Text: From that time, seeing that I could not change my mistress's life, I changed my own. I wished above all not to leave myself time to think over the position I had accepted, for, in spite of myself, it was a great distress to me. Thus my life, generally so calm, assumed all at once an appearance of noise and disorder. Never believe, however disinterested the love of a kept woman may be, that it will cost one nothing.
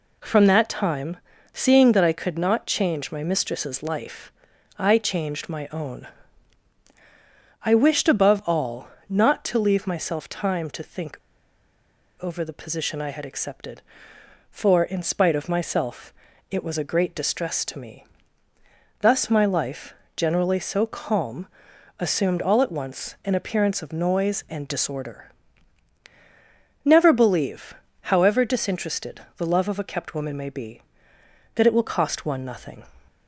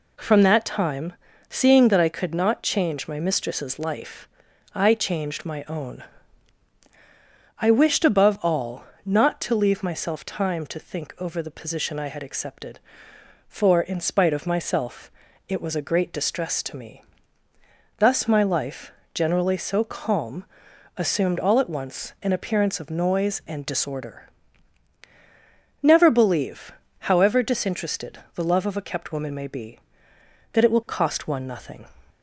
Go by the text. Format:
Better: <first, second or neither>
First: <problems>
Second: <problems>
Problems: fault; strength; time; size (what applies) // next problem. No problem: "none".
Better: second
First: pauses between "all" and "not"; slight; at 8.8 s; 0.22 s long // pauses between "think" and "over"; at 11.1 s; 1.0 s long // pauses between "disinterested" and "the"; slight; at 29.2 s; 0.16 s long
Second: pauses between "all" and "not"; slight; at 8.8 s; 0.22 s long // pauses between "disinterested" and "the"; slight; at 28.1 s; 0.16 s long